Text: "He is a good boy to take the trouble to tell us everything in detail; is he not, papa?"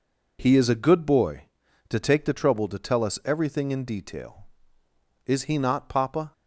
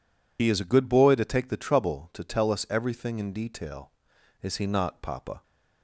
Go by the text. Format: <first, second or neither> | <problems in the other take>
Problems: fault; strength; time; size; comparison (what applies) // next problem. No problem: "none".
first | loses the start of "He"; at 0.3 s; 55 ms